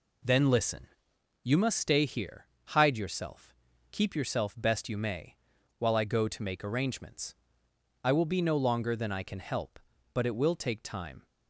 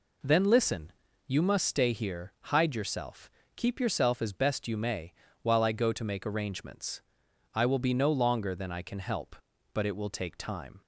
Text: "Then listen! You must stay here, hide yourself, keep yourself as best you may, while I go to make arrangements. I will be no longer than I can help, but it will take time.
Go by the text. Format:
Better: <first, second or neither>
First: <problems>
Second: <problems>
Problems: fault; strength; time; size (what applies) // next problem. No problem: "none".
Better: second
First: skips "as"; at 4.5 s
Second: none